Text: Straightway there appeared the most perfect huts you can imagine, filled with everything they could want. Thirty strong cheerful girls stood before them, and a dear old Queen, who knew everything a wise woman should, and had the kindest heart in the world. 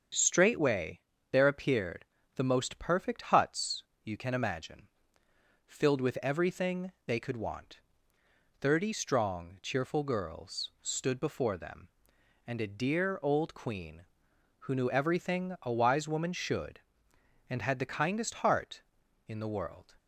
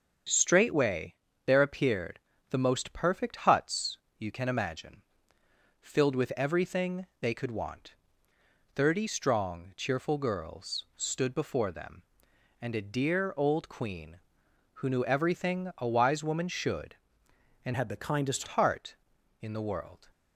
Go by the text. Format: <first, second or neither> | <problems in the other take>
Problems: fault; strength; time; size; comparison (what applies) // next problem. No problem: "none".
first | starts louder than the rest; until 1.6 s; 7 dB; strong in the first // pauses between "Straightway" and "there"; slight; at 1.1 s; 0.32 s long; slight in the first // pauses between "appeared" and "the"; slight; at 2.1 s; 0.30 s long; slight in the first // pauses between "huts" and "you"; slight; at 3.9 s; 0.22 s long; slight in the first // pauses between "everything" and "they"; slight; at 7.0 s; 0.16 s long; slight in the first // changes voice from "had" to "kindest"; from 17.7 to 18.4 s; 0.7 s long